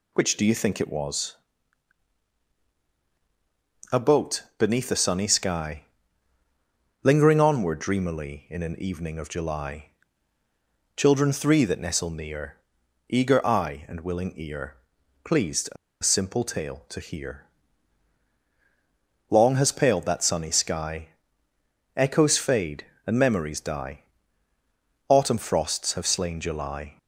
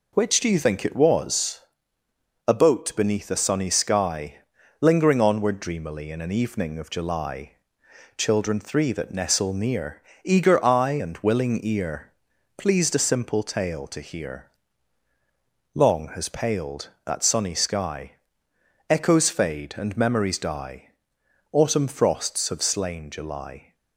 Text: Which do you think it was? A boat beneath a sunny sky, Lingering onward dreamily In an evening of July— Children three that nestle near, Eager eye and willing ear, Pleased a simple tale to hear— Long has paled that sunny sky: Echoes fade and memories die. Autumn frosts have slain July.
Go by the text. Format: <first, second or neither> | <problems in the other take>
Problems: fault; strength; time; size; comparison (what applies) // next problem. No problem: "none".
second | pauses between "boat" and "beneath"; slight; at 4.4 s; 0.16 s long // pauses between "a" and "simple"; slight; at 15.7 s; 0.27 s long